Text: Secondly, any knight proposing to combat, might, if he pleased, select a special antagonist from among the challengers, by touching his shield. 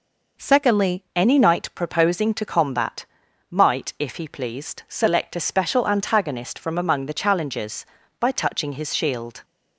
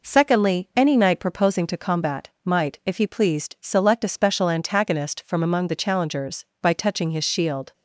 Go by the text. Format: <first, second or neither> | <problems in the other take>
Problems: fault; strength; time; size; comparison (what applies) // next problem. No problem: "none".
second | changes voice at "any"; from 1.1 s on; 8.3 s long